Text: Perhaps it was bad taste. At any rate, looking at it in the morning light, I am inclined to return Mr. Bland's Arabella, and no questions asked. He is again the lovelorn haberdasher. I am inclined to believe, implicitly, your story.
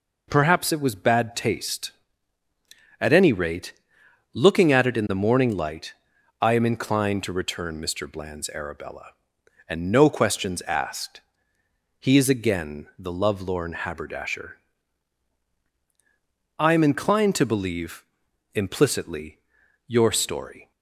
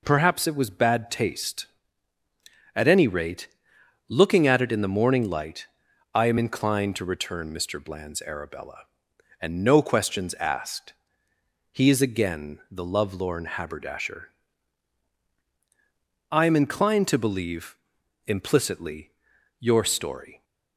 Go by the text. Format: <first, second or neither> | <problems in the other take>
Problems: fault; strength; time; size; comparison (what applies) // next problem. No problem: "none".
neither | none